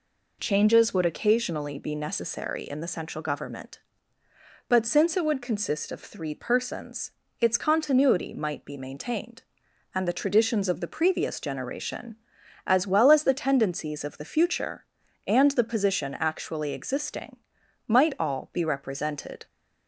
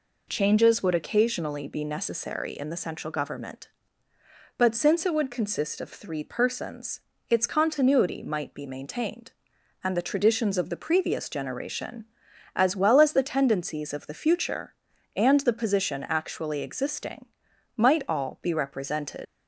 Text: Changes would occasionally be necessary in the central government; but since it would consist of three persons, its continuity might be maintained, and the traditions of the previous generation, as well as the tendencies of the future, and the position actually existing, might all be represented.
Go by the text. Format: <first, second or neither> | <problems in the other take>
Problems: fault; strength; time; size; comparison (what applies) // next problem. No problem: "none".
first | leaves "represented" unfinished; at 19.2 s; 95 ms